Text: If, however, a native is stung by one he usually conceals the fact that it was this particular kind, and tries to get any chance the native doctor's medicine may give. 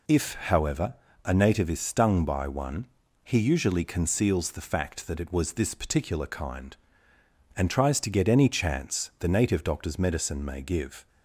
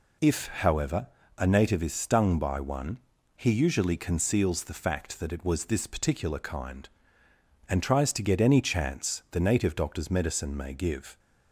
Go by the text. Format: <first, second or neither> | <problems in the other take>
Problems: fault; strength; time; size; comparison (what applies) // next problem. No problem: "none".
neither | pauses between "one" and "he"; the same in both